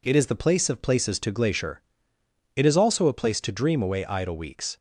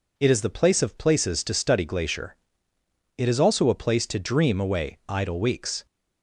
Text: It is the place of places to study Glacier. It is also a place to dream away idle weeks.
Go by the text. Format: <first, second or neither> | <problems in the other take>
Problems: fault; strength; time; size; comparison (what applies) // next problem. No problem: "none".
second | skips "study"; at 1.3 s